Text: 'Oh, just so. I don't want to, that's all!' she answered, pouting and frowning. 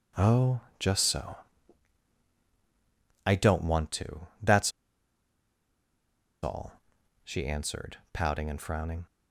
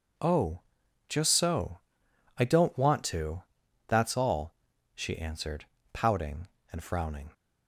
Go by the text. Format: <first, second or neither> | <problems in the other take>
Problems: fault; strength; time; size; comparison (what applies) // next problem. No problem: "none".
second | pauses between "that's" and "all"; strong; at 4.7 s; 1.7 s long